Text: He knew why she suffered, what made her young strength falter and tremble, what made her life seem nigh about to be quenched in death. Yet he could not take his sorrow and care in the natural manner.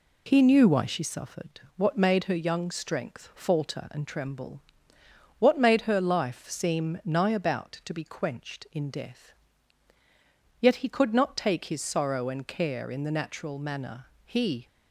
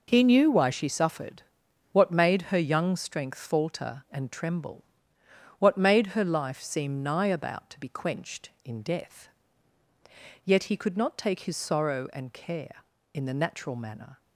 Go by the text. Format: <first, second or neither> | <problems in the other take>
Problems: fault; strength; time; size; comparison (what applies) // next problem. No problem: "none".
second | goes on to say "He"; slight; from 14.2 s on; 0.42 s long